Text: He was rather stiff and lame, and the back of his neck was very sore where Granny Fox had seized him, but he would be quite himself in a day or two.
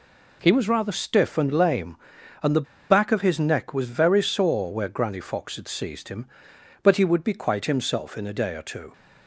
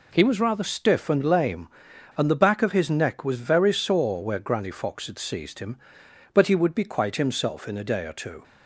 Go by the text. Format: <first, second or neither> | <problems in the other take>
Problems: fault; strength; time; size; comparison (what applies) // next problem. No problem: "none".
second | pauses between "the" and "back"; slight; at 2.6 s; 0.24 s long